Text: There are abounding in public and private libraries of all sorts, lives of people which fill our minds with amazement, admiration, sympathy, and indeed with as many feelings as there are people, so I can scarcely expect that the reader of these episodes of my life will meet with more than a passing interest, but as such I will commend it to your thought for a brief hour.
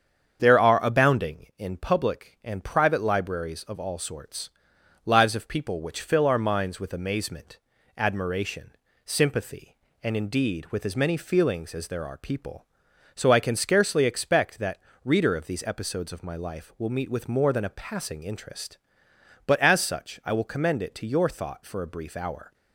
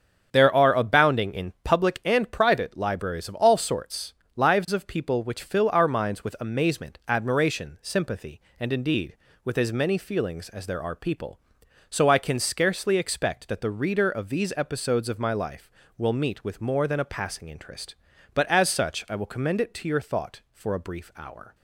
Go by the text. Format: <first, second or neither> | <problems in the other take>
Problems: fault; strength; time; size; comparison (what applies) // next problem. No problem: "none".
second | starts louder than the rest; strong; until 1.4 s; 7.5 dB; also in the second // skips "the"; at 14.9 s